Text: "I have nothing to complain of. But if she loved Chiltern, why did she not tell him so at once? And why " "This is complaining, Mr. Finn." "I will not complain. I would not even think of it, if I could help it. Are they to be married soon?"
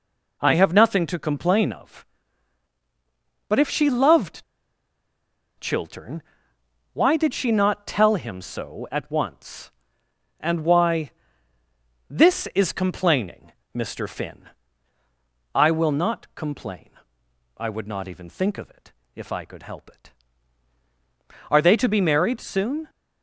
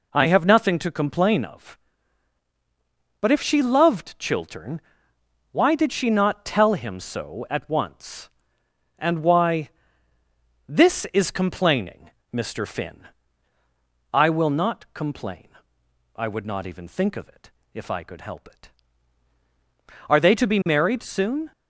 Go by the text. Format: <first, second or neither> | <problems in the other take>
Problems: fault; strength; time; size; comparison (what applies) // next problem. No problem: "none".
second | pauses between "loved" and "Chiltern"; at 4.4 s; 1.1 s long